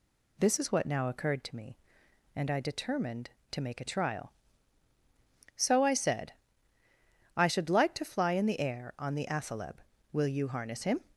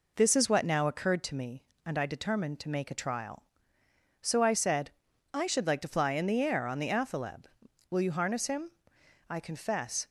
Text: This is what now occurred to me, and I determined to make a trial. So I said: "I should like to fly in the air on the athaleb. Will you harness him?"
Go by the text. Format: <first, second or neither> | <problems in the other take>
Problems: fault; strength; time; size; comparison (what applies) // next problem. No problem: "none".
first | goes on to say "I confess"; noticeable; from 9.3 s on; 0.78 s long